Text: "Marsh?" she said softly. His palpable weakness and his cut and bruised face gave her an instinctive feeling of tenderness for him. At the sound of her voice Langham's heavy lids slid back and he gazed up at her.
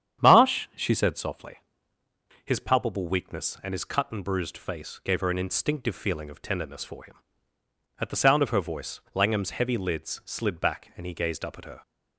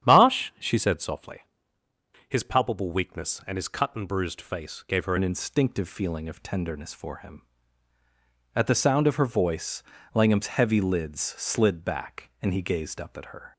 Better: first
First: starts louder than the rest; strong; until 1.3 s; 9 dB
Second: starts louder than the rest; strong; until 1.1 s; 10 dB // changes voice at "an"; from 5.1 s on; 8.4 s long // pauses between "voice" and "Langham's"; slight; at 9.8 s; 0.32 s long

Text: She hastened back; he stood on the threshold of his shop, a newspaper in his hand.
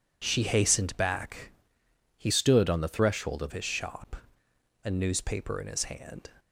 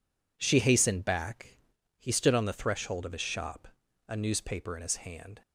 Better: second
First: changes voice from "stood" to "of"; from 2.3 to 3.5 s; 1.2 s long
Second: none

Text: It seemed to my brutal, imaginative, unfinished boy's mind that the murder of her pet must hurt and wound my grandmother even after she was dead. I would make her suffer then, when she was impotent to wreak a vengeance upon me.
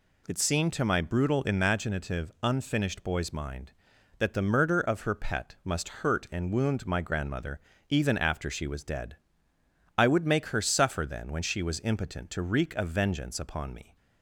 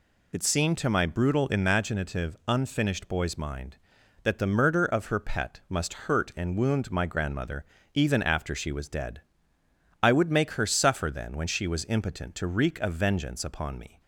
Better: first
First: pauses between "grandmother" and "even"; slight; at 7.5 s; 0.30 s long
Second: loses the start of "It"; at 0.3 s; 25 ms // pauses between "grandmother" and "even"; slight; at 7.6 s; 0.30 s long

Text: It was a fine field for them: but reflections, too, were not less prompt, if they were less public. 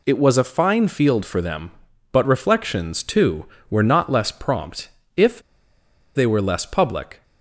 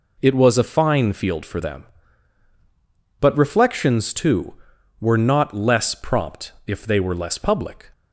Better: second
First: pauses between "if" and "they"; noticeable; at 5.3 s; 0.76 s long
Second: none

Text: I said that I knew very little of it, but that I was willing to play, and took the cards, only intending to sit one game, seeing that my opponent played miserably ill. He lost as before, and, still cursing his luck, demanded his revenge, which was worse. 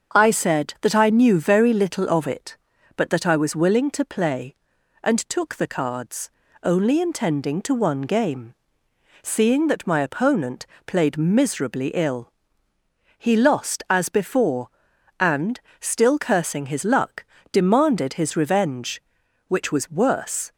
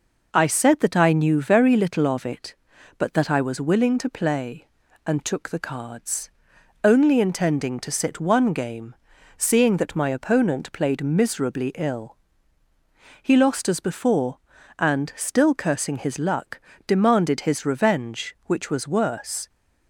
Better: second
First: starts louder than the rest; until 1.2 s; 7 dB // skips "sit"; at 7.7 s // pauses between "opponent" and "played"; slight; at 10.6 s; 0.20 s long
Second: none

